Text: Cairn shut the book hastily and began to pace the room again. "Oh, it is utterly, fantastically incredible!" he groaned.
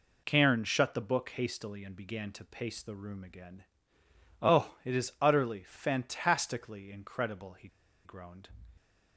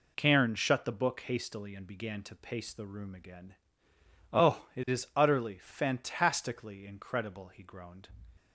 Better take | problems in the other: second | pauses between "he" and "groaned"; at 7.6 s; 0.37 s long

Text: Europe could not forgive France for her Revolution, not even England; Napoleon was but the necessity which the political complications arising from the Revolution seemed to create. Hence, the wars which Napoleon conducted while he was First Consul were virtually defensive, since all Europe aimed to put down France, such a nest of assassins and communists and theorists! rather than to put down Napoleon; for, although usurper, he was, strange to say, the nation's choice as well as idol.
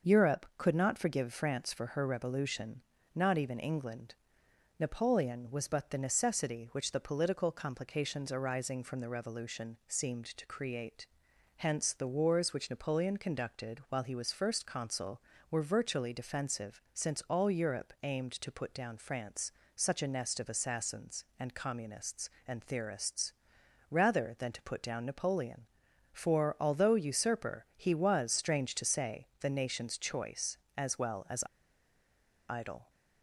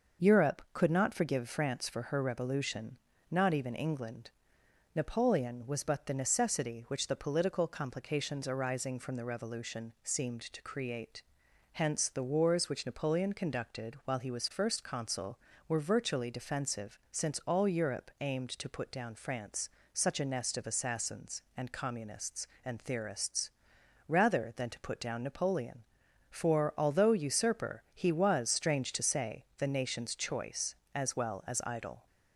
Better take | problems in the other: second | starts louder than the rest; noticeable; until 1.2 s; 6 dB; noticeable in the second // pauses between "as" and "idol"; at 31.4 s; 1.0 s long

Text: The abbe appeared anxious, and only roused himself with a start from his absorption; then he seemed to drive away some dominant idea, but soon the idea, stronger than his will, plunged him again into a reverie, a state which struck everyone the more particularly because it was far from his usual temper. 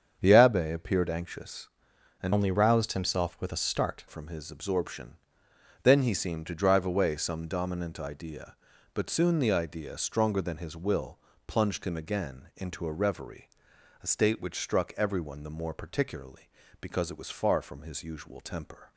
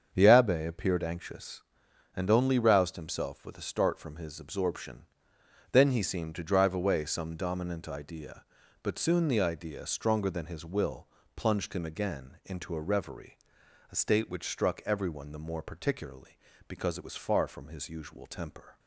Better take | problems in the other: second | starts louder than the rest; strong; until 1.2 s; 7.5 dB; strong in the second // changes voice from "only" to "start"; from 2.3 to 4.0 s; 1.7 s long

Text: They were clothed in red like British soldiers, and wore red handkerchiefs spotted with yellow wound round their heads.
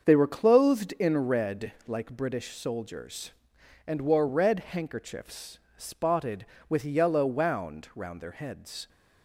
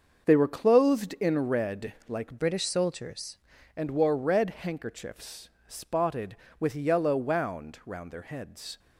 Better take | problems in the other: first | starts louder than the rest; until 1.2 s; 6.5 dB; also in the first // pauses between "red" and "like"; slight; at 1.9 s; 0.16 s long; slight in the first // changes voice from "British" to "soldiers"; from 2.3 to 3.3 s; 1.0 s long // pauses between "handkerchiefs" and "spotted"; slight; at 5.5 s; 0.16 s long; slight in the first

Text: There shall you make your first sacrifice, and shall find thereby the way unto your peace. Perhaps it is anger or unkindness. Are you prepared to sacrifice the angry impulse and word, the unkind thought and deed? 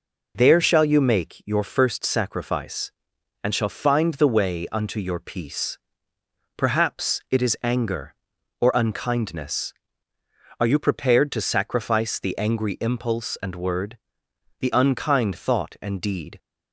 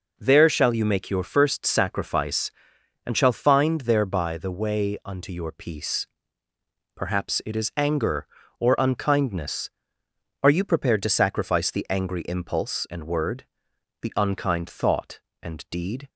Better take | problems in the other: second | skips "thereby"; at 4.1 s

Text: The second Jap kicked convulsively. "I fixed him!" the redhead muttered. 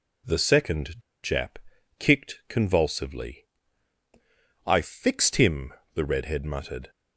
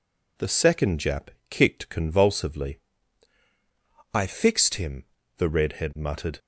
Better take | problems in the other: second | pauses between "second" and "Jap"; slight; at 0.9 s; 0.24 s long // pauses between "Jap" and "kicked"; at 1.5 s; 0.42 s long; slight in the second

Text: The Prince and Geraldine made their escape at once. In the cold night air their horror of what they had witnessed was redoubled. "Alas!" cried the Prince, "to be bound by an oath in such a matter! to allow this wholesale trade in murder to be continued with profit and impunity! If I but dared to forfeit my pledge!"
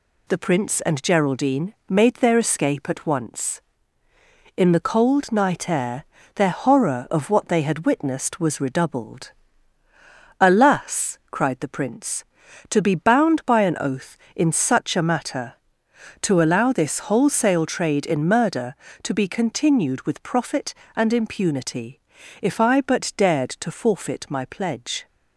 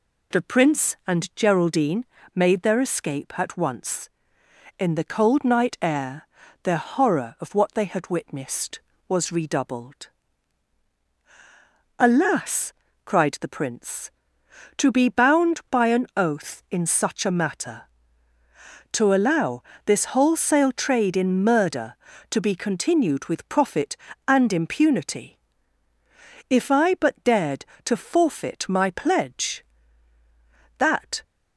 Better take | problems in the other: first | pauses between "Geraldine" and "made"; slight; at 2.0 s; 0.28 s long // pauses between "air" and "their"; at 6.2 s; 0.38 s long; slight in the first // pauses between "allow" and "this"; slight; at 19.6 s; 0.24 s long // goes on to say "That"; slight; from 30.7 s on; 0.44 s long

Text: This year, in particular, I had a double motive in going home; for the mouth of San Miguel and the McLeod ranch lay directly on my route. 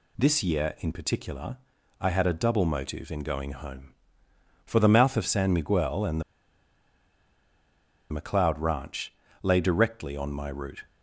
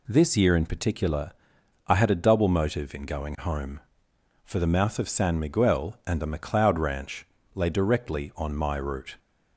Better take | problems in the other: second | pauses between "and" and "the"; strong; at 6.2 s; 1.8 s long // pauses between "ranch" and "lay"; slight; at 9.1 s; 0.28 s long; slight in the second

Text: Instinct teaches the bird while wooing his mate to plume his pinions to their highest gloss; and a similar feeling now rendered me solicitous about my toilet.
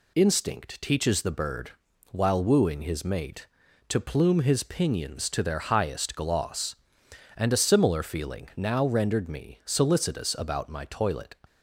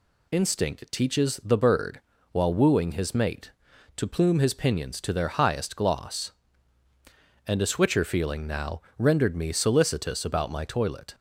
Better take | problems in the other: first | pauses between "bird" and "while"; slight; at 2.0 s; 0.32 s long; also in the first // says "switcher" for "similar"; at 7.6 s // pauses between "now" and "rendered"; slight; at 8.8 s; 0.16 s long

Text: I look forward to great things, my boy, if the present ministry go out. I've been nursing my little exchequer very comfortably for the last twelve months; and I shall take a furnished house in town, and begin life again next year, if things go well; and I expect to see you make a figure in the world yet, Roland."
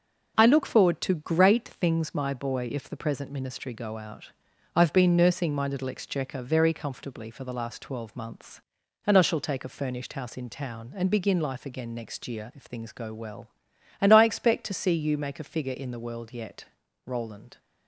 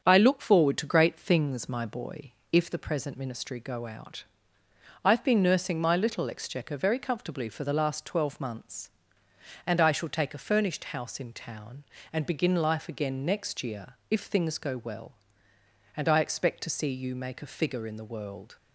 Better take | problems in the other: first | starts louder than the rest; strong; until 1.0 s; 7.5 dB // stops before "yet Roland"; at 18.5 s

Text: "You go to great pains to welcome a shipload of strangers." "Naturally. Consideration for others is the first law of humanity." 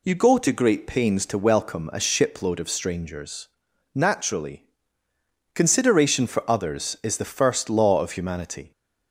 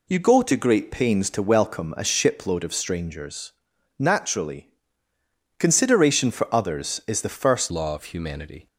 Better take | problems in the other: first | changes voice at "law"; from 7.7 s on; 0.9 s long

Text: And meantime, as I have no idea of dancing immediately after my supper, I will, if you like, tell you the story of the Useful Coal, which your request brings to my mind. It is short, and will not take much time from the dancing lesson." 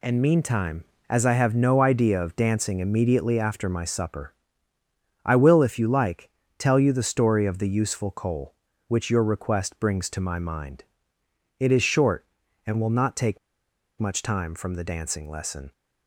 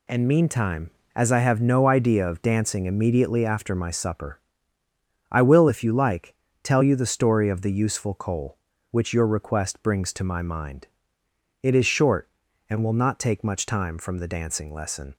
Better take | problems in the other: second | pauses between "take" and "much"; noticeable; at 13.3 s; 0.61 s long

